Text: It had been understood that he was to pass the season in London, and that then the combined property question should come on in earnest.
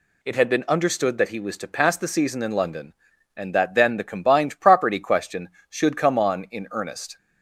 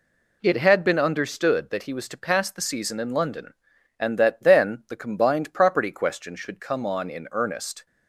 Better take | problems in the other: neither | none

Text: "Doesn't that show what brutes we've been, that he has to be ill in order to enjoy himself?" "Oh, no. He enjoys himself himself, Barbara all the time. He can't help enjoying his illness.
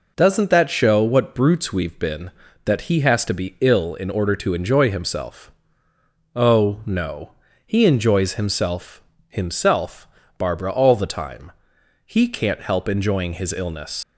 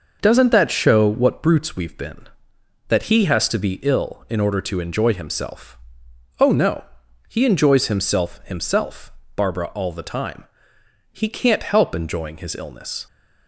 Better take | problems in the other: second | pauses between "himself" and "himself"; slight; at 9.0 s; 0.26 s long // leaves "illness" unfinished; at 14.0 s; 90 ms

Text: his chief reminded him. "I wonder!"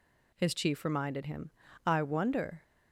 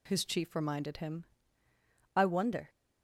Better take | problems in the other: neither | none

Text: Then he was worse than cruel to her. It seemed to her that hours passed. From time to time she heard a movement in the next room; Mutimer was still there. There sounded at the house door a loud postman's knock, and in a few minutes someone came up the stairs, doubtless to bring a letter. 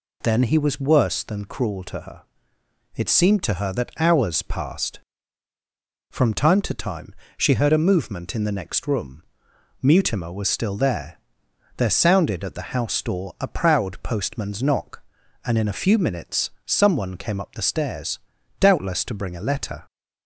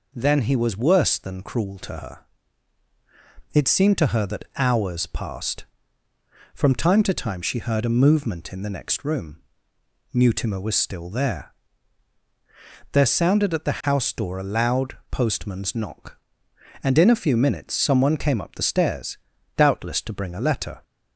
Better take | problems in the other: second | pauses between "time" and "she"; slight; at 7.1 s; 0.24 s long // says "proud" for "loud"; at 13.4 s // pauses between "minutes" and "someone"; slight; at 16.4 s; 0.16 s long

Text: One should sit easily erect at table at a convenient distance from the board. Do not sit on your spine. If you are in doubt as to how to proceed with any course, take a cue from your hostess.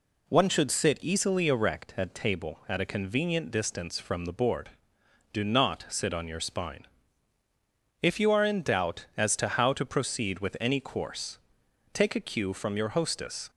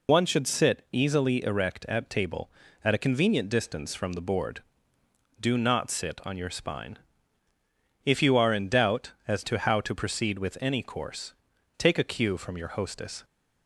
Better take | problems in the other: first | loses the start of "One"; at 0.0 s; 70 ms

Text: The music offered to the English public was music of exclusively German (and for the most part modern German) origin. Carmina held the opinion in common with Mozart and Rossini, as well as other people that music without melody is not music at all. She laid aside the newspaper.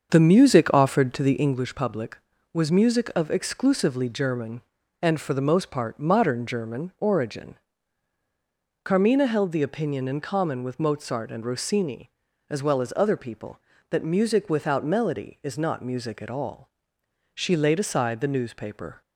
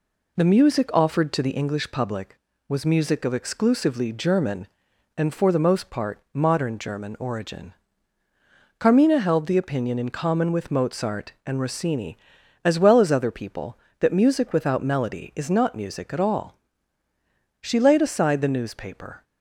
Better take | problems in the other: second | starts louder than the rest; until 1.6 s; 7 dB

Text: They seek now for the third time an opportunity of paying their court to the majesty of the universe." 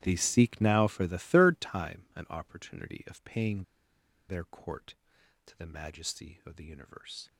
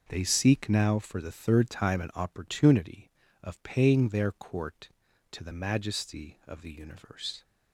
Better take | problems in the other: second | starts louder than the rest; strong; until 1.0 s; 13 dB // pauses between "paying" and "their"; noticeable; at 3.6 s; 0.67 s long

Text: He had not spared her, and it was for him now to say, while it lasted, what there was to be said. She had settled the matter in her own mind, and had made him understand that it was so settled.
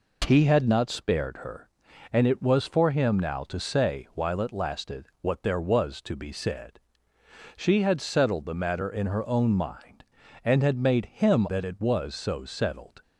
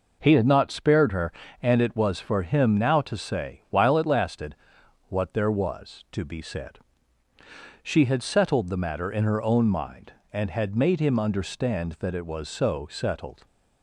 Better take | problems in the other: second | skips "understand"; at 11.4 s

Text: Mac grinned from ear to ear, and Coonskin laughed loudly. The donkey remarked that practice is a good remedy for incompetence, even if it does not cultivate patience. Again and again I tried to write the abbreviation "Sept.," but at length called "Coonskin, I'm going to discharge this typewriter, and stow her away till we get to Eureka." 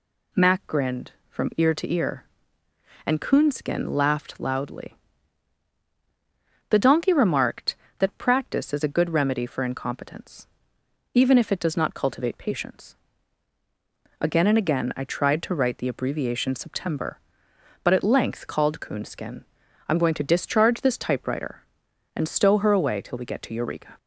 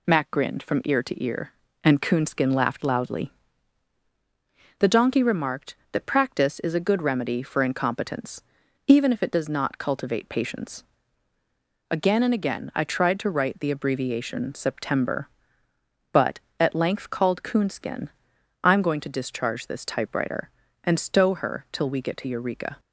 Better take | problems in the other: first | skips "away"; at 21.6 s

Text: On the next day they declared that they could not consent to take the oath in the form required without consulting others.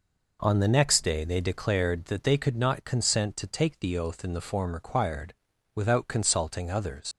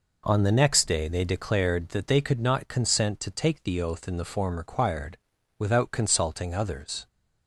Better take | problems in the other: second | pauses between "required" and "without"; at 5.3 s; 0.40 s long; also in the second // leaves "others" unfinished; at 7.1 s; 110 ms

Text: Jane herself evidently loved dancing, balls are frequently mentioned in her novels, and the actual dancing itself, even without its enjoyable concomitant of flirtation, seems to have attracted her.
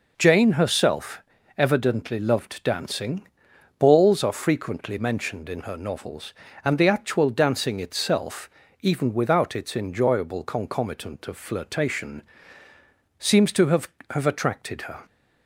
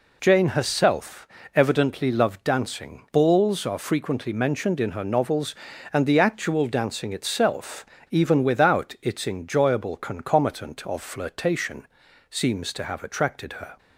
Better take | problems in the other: second | pauses between "herself" and "evidently"; slight; at 1.2 s; 0.36 s long; slight in the second // says "have" twice; at 14.0 s

